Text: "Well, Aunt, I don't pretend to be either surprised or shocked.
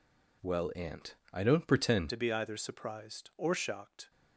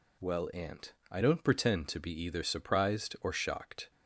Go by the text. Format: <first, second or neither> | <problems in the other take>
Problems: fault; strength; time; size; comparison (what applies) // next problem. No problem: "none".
second | changes voice at "to"; from 2.1 s on; 2.0 s long